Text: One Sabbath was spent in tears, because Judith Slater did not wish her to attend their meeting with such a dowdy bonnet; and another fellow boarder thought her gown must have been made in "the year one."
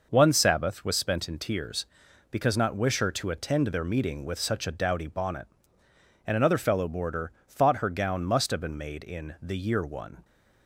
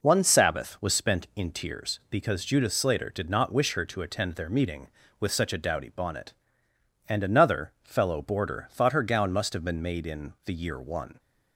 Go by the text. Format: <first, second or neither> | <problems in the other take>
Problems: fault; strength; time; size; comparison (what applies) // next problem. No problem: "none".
second | skips "Judith Slater did"; at 2.5 s // pauses between "boarder" and "thought"; slight; at 7.3 s; 0.16 s long